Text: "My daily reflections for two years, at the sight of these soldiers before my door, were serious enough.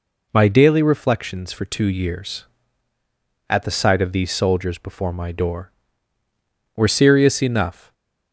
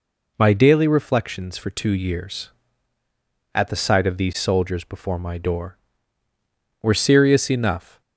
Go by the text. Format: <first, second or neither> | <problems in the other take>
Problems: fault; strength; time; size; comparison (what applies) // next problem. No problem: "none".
neither | none